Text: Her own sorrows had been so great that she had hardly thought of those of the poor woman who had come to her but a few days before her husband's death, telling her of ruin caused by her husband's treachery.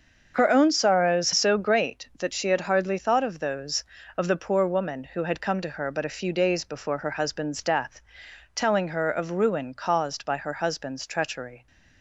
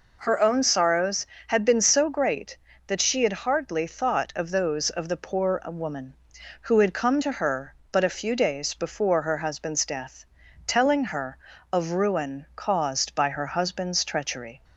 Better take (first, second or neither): second